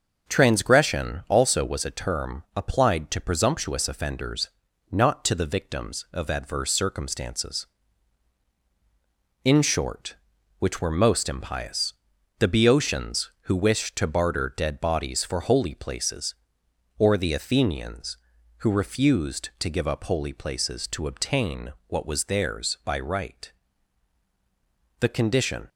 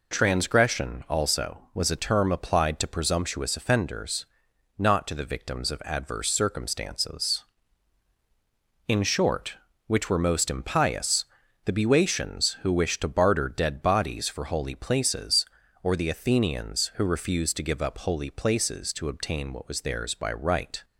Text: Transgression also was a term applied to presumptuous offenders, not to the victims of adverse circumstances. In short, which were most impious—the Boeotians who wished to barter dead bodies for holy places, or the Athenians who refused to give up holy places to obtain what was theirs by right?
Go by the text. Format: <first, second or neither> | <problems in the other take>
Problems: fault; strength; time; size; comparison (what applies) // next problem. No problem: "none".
second | starts louder than the rest; noticeable; until 1.3 s; 6 dB // goes on to say "The condition"; noticeable; from 25.0 s on; 0.68 s long